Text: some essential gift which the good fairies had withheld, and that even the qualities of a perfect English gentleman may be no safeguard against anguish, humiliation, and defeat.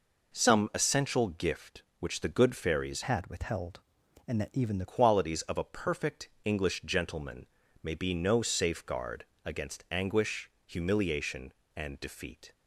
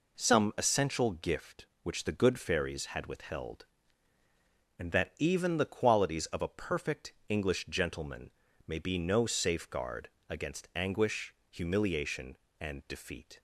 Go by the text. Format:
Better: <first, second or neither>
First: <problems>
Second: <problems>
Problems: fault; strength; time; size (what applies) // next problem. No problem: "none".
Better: second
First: changes voice from "had" to "the"; from 3.0 to 4.8 s; 1.8 s long // pauses between "perfect" and "English"; slight; at 6.2 s; 0.16 s long // pauses between "gentleman" and "may"; slight; at 7.4 s; 0.36 s long // pauses between "safeguard" and "against"; slight; at 9.2 s; 0.22 s long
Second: pauses between "perfect" and "English"; slight; at 7.1 s; 0.16 s long // pauses between "gentleman" and "may"; slight; at 8.3 s; 0.36 s long // pauses between "safeguard" and "against"; slight; at 10.0 s; 0.22 s long